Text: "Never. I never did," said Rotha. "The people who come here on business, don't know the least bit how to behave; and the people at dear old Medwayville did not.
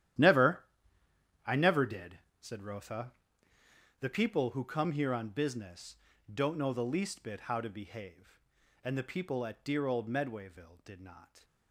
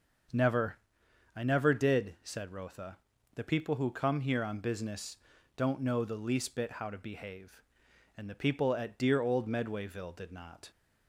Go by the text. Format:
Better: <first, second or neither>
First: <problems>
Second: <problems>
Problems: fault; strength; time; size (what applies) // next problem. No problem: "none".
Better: second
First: gets quieter; strong; throughout; 14.5 dB // starts louder than the rest; strong; until 2.0 s; 11.5 dB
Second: starts louder than the rest; until 1.8 s; 6 dB